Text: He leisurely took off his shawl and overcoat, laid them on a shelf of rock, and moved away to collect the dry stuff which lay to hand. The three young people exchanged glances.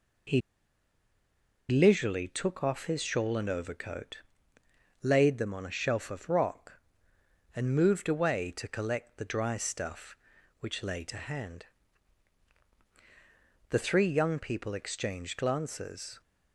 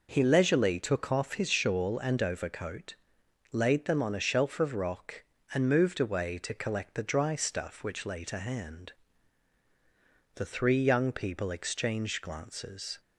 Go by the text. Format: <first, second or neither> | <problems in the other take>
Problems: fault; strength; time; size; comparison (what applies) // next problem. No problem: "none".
second | pauses between "He" and "leisurely"; strong; at 0.4 s; 1.2 s long